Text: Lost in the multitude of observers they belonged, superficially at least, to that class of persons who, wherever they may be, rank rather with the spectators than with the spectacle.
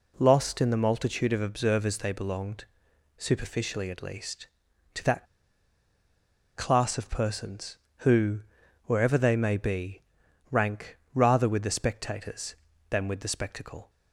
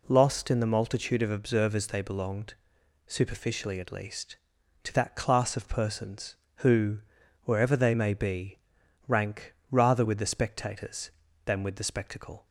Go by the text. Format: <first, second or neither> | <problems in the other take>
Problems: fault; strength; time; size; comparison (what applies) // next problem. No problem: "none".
second | pauses between "that" and "class"; strong; at 5.2 s; 1.3 s long // pauses between "rank" and "rather"; slight; at 10.9 s; 0.16 s long; slight in the second